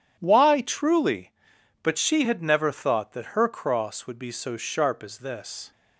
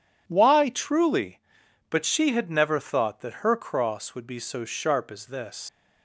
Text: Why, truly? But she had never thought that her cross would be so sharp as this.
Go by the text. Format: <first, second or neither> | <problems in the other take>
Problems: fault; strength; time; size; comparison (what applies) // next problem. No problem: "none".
first | leaves "this" unfinished; at 5.6 s; 100 ms